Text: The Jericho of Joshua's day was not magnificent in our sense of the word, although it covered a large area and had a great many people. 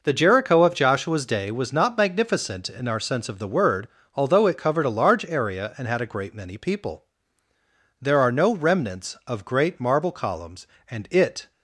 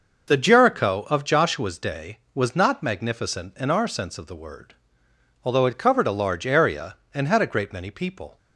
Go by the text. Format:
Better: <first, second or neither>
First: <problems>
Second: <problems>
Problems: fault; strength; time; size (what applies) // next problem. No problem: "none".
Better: second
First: goes on to say "There are no remnants of great marble columns and it"; strong; from 8.0 s on; 3.5 s long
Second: none